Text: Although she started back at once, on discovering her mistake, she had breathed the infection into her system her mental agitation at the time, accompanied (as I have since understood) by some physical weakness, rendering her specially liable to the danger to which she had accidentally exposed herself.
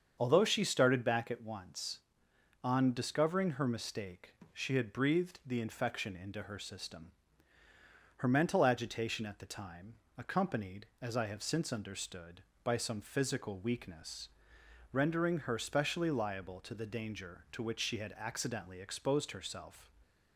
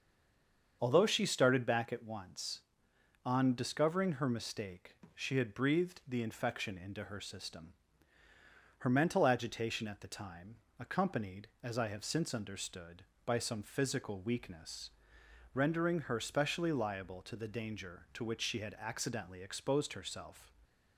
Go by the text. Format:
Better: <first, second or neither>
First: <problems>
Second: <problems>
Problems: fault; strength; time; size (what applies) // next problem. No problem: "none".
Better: first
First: starts louder than the rest; until 1.2 s; 7 dB // pauses between "system" and "her"; at 7.1 s; 1.0 s long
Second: stays silent before the first word; slight; until 0.8 s; 0.8 s long // starts louder than the rest; until 1.8 s; 7 dB // pauses between "system" and "her"; at 7.7 s; 1.0 s long